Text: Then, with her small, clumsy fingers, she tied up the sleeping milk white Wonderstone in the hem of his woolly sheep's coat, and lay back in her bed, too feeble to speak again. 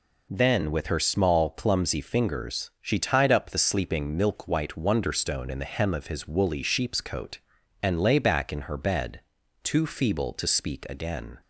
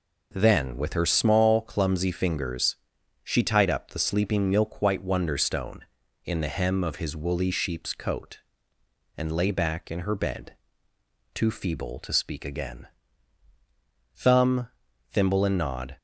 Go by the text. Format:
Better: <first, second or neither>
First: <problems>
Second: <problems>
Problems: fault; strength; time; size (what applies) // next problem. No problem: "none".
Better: first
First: none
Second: goes on to say "Thumb Thimble and Nod"; strong; from 14.1 s on; 1.8 s long